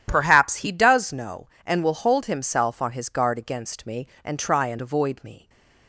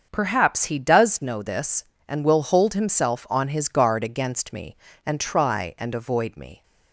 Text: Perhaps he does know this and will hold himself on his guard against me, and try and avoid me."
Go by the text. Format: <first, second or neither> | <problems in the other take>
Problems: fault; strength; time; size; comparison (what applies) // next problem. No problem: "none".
second | starts louder than the rest; strong; until 1.0 s; 10.5 dB; also in the second // skips "this"; at 1.5 s // stays silent after the last word; slight; from 5.3 s on; 0.5 s long